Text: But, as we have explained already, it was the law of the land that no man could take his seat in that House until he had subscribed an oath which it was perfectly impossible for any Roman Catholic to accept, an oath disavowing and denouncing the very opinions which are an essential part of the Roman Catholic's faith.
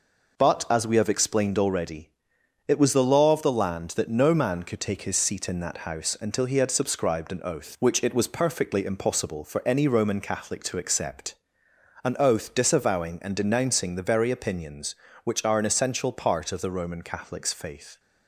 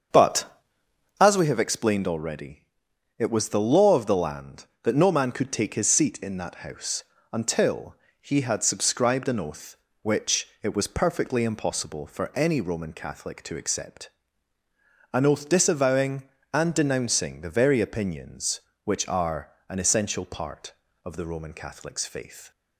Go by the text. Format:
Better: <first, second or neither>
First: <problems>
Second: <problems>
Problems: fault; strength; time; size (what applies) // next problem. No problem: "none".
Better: first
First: none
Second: starts louder than the rest; until 1.5 s; 7 dB // pauses between "House" and "until"; slight; at 7.0 s; 0.28 s long // pauses between "until" and "he"; slight; at 7.9 s; 0.26 s long // pauses between "are" and "an"; slight; at 19.5 s; 0.18 s long